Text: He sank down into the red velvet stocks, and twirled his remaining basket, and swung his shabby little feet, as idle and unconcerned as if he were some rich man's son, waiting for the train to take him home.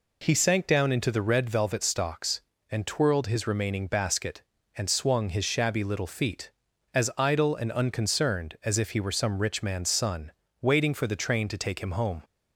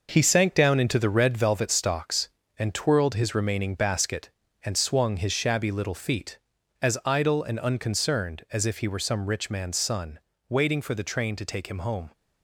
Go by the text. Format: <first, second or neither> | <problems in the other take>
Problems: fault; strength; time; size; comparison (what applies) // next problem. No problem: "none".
first | gets quieter; strong; throughout; 7.5 dB